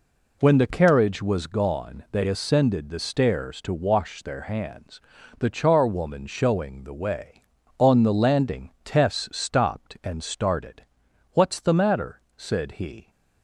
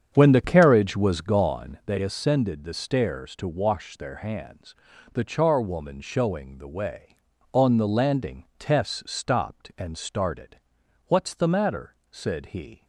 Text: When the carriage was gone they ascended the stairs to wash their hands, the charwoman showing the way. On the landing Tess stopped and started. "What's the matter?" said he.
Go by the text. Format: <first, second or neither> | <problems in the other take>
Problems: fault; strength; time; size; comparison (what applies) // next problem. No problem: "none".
first | starts louder than the rest; strong; until 1.8 s; 8 dB